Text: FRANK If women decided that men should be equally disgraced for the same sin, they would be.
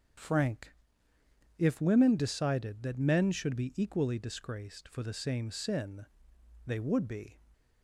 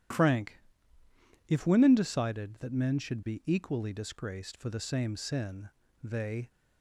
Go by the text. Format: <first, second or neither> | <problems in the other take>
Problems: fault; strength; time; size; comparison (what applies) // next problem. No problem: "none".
first | starts louder than the rest; strong; until 2.0 s; 11 dB; strong in the first // pauses between "FRANK" and "If"; noticeable; at 0.5 s; 0.88 s long; noticeable in the first // stops before "would be"; at 6.4 s